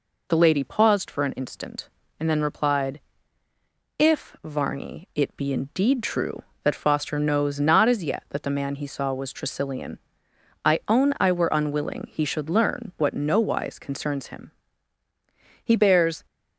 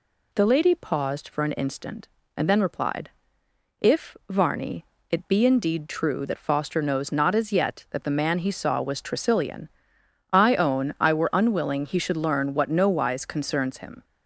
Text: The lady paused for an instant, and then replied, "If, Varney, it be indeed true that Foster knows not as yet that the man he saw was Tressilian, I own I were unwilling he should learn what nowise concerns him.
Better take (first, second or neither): second